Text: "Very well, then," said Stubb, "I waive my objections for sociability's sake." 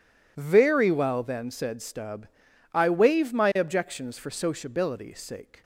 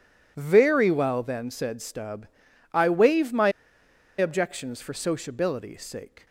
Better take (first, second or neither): first